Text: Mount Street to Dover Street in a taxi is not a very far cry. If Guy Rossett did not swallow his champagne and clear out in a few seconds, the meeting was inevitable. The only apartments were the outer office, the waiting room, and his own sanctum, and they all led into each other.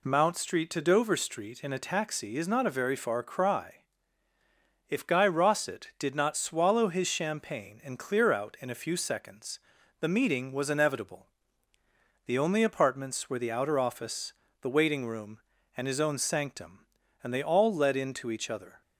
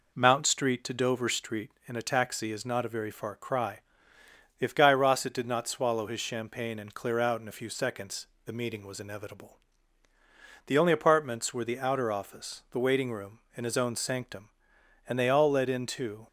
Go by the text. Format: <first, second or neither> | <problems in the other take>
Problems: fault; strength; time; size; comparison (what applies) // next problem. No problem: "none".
first | stops before "each other"; at 16.2 s